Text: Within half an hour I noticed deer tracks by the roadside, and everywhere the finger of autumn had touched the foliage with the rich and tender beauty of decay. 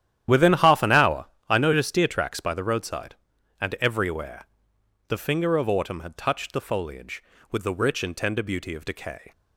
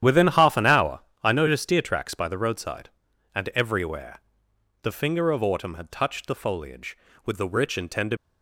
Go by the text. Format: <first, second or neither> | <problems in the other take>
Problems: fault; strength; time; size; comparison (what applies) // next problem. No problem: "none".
first | starts louder than the rest; strong; until 1.2 s; 10.5 dB; strong in the first // pauses between "hour" and "I"; slight; at 0.9 s; 0.22 s long; slight in the first // pauses between "everywhere" and "the"; noticeable; at 4.1 s; 0.64 s long; noticeable in the first // stops before "beauty of decay"; at 8.1 s